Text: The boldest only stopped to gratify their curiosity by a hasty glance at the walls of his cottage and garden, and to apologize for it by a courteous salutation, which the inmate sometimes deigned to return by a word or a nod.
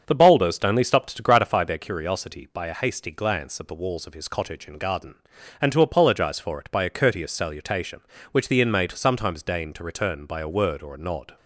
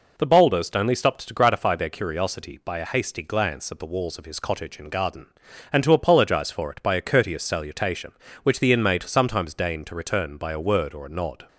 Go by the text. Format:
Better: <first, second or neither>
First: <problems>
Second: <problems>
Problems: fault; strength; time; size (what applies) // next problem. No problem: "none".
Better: second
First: starts louder than the rest; until 1.8 s; 6.5 dB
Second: none